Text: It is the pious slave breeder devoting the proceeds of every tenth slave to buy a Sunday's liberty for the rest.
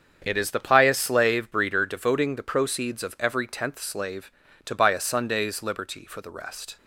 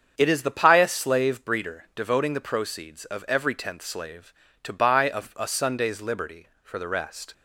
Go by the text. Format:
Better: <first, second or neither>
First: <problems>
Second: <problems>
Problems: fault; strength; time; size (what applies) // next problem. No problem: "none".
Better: first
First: starts louder than the rest; strong; until 1.2 s; 7.5 dB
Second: starts louder than the rest; strong; until 1.1 s; 7.5 dB // says "a" twice; at 5.3 s